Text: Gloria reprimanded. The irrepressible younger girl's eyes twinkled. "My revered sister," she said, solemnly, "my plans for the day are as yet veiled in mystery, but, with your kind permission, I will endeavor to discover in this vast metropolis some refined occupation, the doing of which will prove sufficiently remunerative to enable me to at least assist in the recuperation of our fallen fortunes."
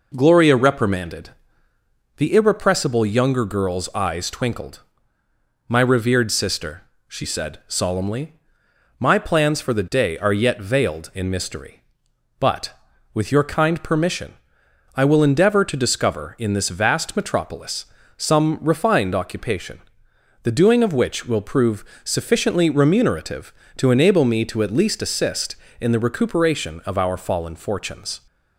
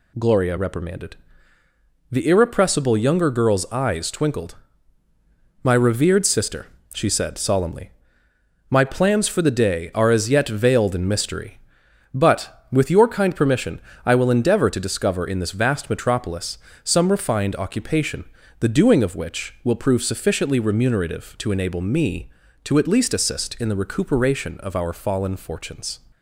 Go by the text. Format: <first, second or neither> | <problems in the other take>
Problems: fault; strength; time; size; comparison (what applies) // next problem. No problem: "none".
second | skips "as"; at 10.3 s // pauses between "metropolis" and "some"; slight; at 17.8 s; 0.32 s long; slight in the second // pauses between "prove" and "sufficiently"; slight; at 21.8 s; 0.20 s long